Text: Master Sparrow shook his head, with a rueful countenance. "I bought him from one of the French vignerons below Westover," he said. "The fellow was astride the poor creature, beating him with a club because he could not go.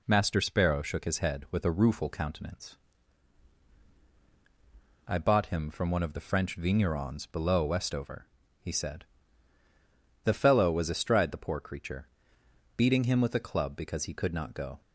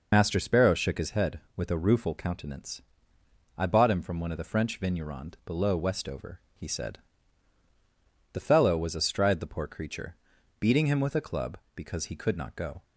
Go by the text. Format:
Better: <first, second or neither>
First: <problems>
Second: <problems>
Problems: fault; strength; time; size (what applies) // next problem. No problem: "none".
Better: first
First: none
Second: loses the start of "Master"; at 0.1 s; 55 ms